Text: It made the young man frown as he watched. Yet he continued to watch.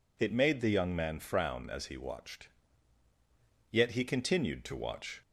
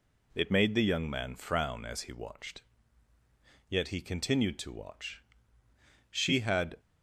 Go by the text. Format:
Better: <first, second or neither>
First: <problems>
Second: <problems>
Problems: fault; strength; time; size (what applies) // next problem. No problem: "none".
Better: first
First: none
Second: goes on to say "She had"; noticeable; from 6.1 s on; 0.68 s long